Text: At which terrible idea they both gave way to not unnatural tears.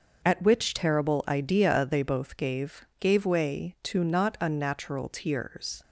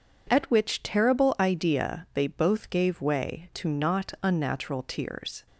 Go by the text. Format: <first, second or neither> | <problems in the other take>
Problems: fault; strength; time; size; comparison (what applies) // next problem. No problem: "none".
second | says "gave" twice; at 3.0 s